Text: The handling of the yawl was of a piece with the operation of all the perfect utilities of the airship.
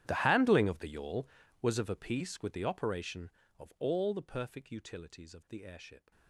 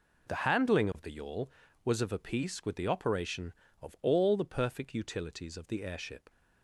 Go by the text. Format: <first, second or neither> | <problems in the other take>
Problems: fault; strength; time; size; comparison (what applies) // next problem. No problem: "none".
second | gets quieter; strong; throughout; 22.5 dB